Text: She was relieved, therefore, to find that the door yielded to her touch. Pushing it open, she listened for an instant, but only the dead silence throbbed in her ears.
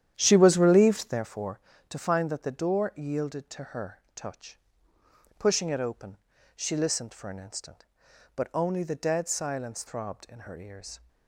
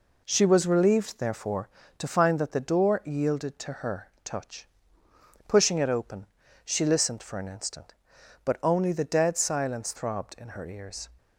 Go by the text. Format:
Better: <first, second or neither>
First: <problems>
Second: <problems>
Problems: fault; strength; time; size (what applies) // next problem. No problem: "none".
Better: second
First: starts louder than the rest; strong; until 1.2 s; 10.5 dB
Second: none